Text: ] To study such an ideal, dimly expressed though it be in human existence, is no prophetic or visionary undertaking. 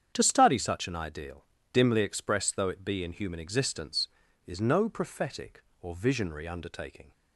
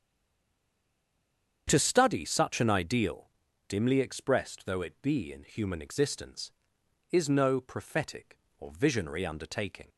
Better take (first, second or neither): first